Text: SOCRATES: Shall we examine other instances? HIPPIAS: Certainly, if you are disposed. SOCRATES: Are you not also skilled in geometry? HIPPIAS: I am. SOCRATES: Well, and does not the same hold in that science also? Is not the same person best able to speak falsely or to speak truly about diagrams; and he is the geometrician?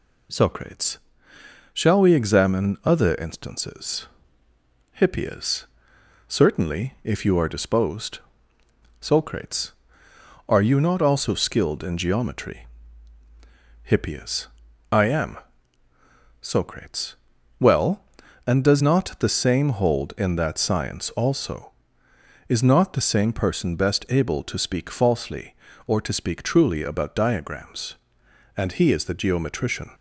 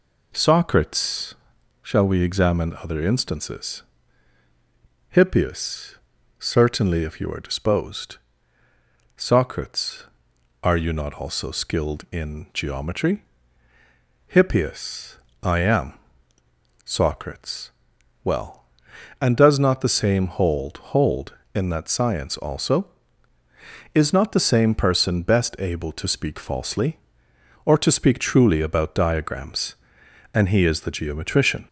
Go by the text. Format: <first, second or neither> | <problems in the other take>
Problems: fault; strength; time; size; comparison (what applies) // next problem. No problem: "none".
first | says "hold" twice; at 20.7 s